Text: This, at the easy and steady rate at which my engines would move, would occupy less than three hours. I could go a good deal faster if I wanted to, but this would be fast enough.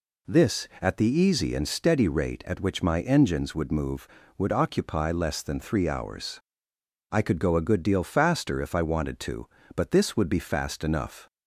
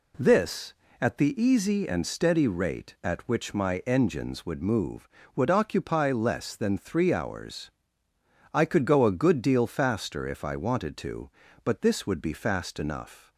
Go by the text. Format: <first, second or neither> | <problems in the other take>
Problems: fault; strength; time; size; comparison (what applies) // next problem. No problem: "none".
neither | none